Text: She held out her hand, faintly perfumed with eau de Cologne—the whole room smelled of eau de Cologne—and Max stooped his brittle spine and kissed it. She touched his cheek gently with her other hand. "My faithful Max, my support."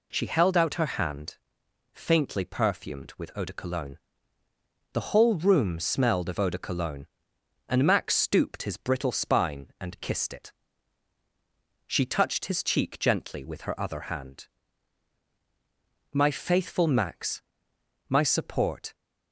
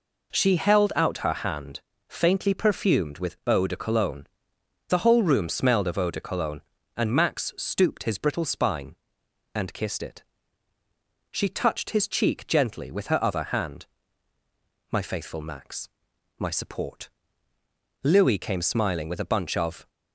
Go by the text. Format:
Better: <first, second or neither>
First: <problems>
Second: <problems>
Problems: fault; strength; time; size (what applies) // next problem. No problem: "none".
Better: first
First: none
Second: goes on to say "Louis came smiling with a bunch of"; strong; from 18.0 s on; 1.8 s long